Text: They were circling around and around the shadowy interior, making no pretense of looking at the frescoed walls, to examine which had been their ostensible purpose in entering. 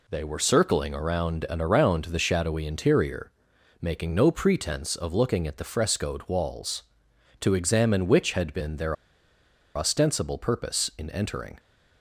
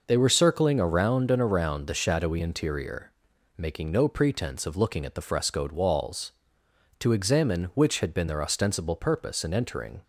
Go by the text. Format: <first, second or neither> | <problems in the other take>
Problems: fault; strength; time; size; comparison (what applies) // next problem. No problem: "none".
second | pauses between "their" and "ostensible"; noticeable; at 8.9 s; 0.81 s long